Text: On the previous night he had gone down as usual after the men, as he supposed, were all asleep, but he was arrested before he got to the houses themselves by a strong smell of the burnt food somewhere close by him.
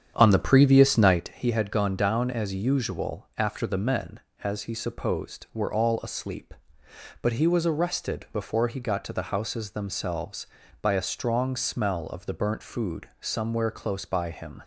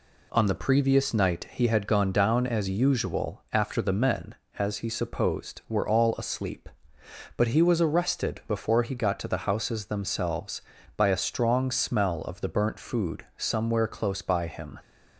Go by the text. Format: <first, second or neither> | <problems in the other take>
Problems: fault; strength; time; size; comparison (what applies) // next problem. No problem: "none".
second | starts louder than the rest; strong; until 1.3 s; 8.5 dB